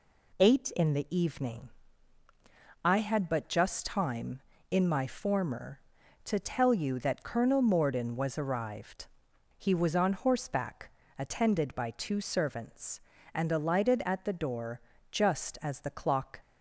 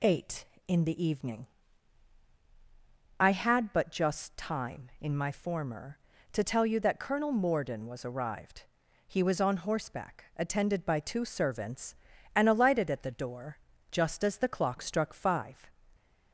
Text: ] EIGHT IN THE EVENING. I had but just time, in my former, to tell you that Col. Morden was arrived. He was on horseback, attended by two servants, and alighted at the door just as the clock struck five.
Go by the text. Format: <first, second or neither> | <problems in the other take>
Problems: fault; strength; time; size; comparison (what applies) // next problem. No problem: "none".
second | pauses between "door" and "just"; slight; at 14.7 s; 0.32 s long; slight in the second // stops before "struck five"; at 16.4 s